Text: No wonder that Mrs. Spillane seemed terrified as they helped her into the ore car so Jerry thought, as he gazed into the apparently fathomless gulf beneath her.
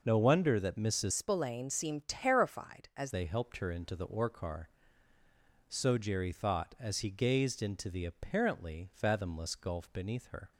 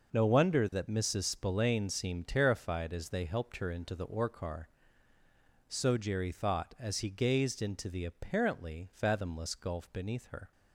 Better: second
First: changes voice from "Spillane" to "as"; from 1.1 to 3.1 s; 2.0 s long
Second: none

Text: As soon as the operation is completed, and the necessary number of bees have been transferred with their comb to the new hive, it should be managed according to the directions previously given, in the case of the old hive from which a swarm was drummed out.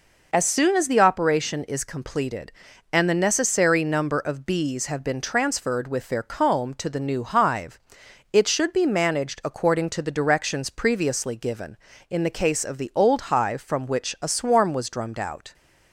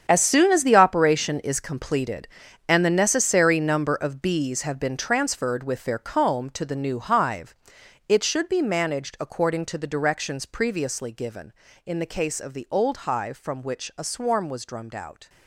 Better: first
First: none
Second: gets quieter; strong; throughout; 13 dB

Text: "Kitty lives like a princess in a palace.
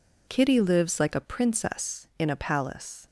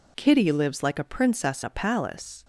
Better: first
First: none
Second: skips "in"; at 1.6 s

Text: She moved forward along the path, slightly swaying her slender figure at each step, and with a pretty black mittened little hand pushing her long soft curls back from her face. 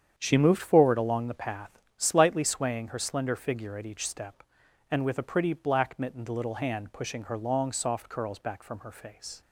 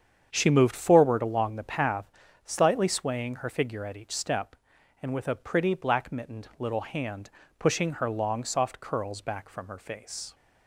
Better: first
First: starts louder than the rest; strong; until 1.1 s; 8 dB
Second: starts louder than the rest; strong; until 1.3 s; 8 dB // skips "slender"; at 3.4 s // pauses between "hand" and "pushing"; slight; at 7.3 s; 0.26 s long

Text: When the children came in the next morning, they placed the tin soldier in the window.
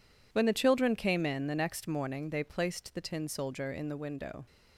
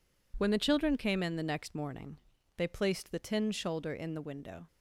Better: first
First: none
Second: says "shoulder" for "soldier"; at 3.5 s

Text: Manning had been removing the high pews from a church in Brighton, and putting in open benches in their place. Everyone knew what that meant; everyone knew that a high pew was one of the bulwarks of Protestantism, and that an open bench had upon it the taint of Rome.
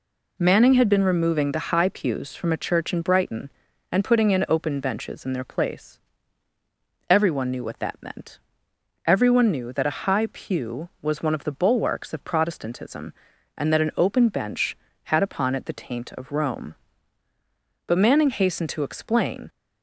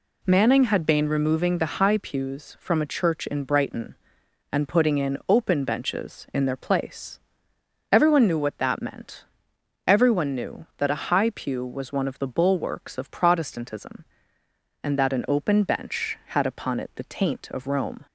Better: second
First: goes on to say "But Manning hastened to explain"; from 17.8 s on; 1.6 s long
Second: none

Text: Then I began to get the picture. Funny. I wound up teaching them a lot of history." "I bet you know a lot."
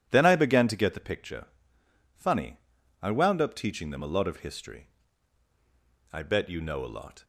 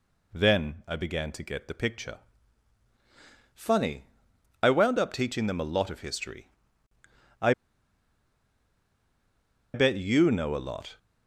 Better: first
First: none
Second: pauses between "I" and "bet"; strong; at 7.5 s; 2.2 s long

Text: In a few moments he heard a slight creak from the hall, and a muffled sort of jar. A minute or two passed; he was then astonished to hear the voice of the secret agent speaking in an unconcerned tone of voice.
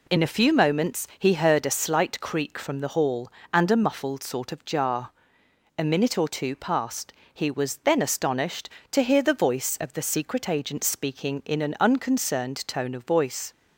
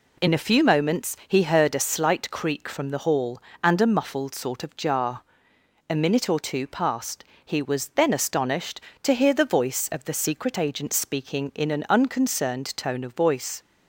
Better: neither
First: none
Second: none

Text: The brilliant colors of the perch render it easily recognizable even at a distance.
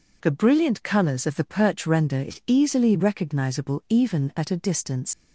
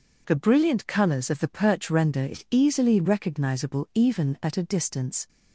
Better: second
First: leaves "distance" unfinished; at 5.1 s; 80 ms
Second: none

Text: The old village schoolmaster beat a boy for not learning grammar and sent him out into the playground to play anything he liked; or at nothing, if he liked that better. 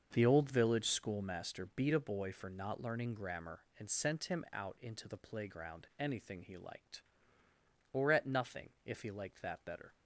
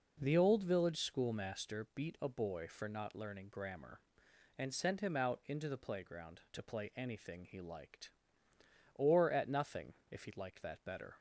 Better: second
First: starts louder than the rest; until 1.1 s; 6.5 dB // skips "to play"; at 5.9 s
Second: none

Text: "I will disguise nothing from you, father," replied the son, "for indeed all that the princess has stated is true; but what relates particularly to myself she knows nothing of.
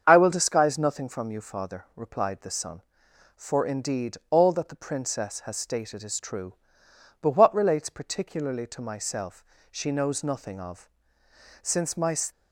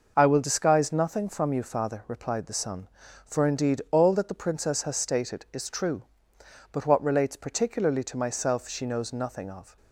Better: second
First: starts louder than the rest; strong; until 1.0 s; 7 dB // pauses between "myself" and "she"; slight; at 9.4 s; 0.28 s long // goes on to say "Since my"; from 11.6 s on; 0.52 s long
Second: none

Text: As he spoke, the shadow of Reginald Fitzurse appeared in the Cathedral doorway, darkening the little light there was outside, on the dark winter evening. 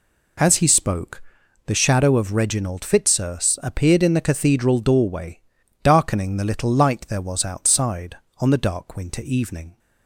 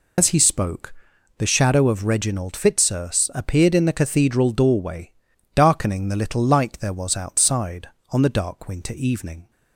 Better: first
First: none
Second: loses the start of "As"; at 0.1 s; 90 ms

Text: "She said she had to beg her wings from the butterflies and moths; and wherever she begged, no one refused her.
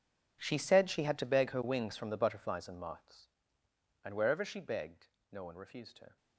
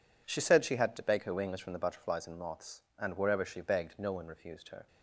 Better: second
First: gets quieter; strong; throughout; 18.5 dB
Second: none

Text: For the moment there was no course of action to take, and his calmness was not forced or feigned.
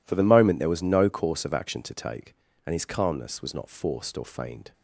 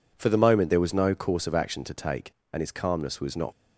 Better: first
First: none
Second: stops before "forced or feigned"; at 3.5 s

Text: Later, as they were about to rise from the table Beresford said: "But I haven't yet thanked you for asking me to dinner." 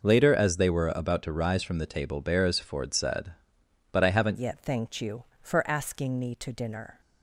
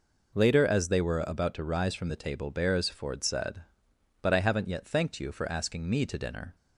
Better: second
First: changes voice at "yet"; from 4.3 s on; 2.7 s long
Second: none

